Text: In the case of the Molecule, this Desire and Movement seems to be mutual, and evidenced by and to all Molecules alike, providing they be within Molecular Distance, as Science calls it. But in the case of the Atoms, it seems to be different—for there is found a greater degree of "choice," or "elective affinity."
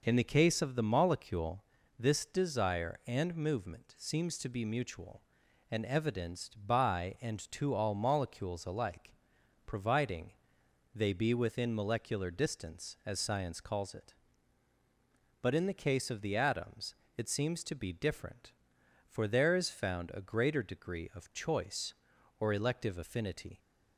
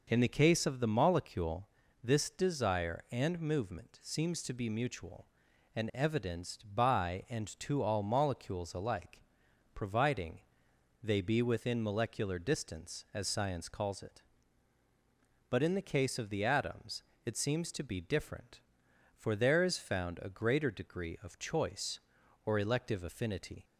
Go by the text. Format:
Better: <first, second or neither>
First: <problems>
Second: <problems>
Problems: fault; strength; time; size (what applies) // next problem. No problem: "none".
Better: neither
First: pauses between "providing" and "they"; noticeable; at 10.3 s; 0.62 s long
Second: pauses between "providing" and "they"; noticeable; at 10.4 s; 0.62 s long